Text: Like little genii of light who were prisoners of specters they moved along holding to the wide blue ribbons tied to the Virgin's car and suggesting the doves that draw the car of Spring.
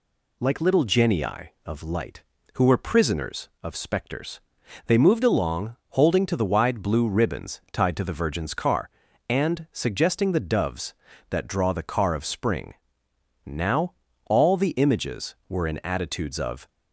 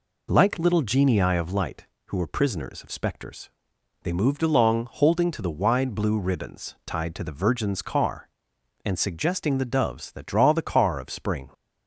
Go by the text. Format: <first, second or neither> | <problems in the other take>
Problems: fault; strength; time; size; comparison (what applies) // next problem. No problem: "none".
second | pauses between "specters" and "they"; noticeable; at 4.3 s; 0.48 s long; noticeable in the second // pauses between "along" and "holding"; slight; at 5.7 s; 0.16 s long // goes on to say "Now all the images were in attitudes of"; strong; from 13.4 s on; 3.2 s long